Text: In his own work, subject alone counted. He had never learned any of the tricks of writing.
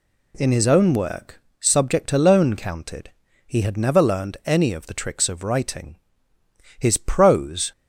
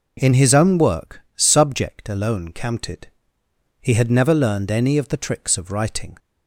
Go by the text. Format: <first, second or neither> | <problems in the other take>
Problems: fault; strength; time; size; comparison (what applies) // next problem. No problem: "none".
second | goes on to say "His prose"; noticeable; from 6.7 s on; 0.94 s long